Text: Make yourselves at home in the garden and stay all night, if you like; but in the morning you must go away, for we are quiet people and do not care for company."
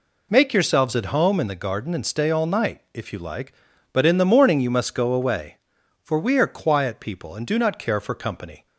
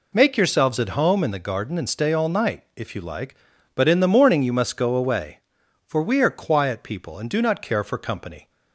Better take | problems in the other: neither | none

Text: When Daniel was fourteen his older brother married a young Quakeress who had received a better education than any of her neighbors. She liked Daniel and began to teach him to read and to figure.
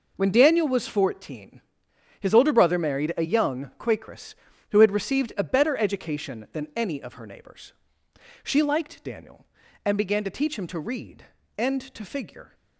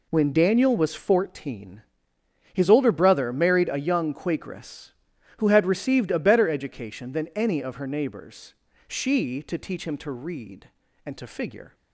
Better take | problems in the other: first | pauses between "fourteen" and "his"; noticeable; at 1.8 s; 0.70 s long; noticeable in the first // skips "liked Daniel and began"; at 9.4 s

